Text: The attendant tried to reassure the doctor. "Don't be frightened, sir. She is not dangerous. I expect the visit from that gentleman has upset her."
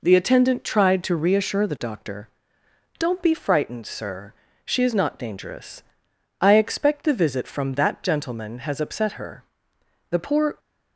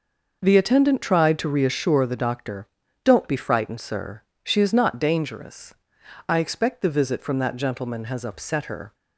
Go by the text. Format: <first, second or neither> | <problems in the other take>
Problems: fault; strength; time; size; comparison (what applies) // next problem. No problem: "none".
second | goes on to say "The poor"; from 10.0 s on; 0.50 s long